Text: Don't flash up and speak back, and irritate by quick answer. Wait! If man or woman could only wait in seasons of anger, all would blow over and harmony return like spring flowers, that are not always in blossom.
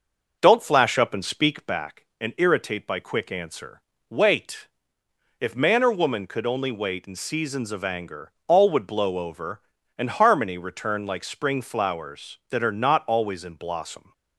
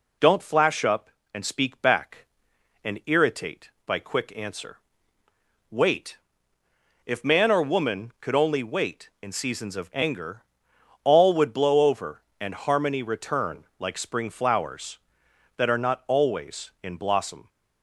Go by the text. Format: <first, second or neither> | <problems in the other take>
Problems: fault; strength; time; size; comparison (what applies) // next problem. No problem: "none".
second | starts louder than the rest; noticeable; until 2.0 s; 6 dB